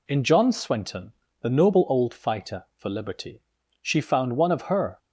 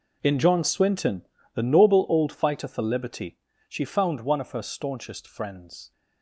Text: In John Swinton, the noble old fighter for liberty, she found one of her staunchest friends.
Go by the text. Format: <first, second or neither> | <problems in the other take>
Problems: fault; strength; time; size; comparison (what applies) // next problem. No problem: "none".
second | stops before "staunchest friends"; at 4.9 s